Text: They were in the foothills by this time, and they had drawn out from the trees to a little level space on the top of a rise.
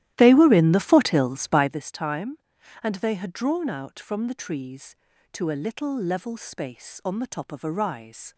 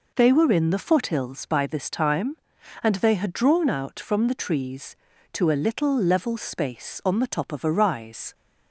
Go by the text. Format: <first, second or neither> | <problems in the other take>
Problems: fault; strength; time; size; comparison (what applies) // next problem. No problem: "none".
second | starts louder than the rest; strong; until 1.8 s; 13.5 dB